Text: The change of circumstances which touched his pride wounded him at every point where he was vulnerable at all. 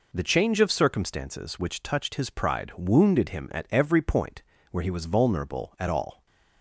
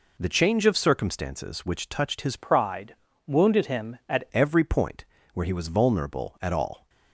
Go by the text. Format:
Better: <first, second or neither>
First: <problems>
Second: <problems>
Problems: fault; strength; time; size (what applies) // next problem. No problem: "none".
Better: first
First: pauses between "point" and "where"; slight; at 4.4 s; 0.30 s long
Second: changes voice from "pride" to "at"; from 2.3 to 4.2 s; 1.9 s long // pauses between "pride" and "wounded"; slight; at 2.9 s; 0.30 s long // pauses between "point" and "where"; slight; at 5.0 s; 0.30 s long